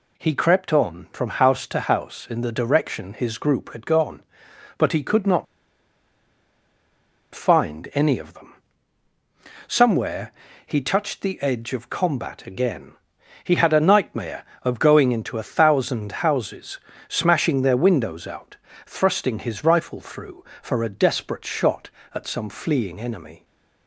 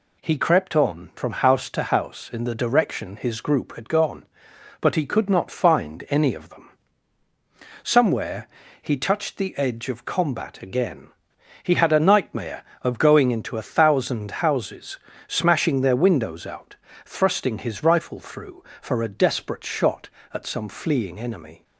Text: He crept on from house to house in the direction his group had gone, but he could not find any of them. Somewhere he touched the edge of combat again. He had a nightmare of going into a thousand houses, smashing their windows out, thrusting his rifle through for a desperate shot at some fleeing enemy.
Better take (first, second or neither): second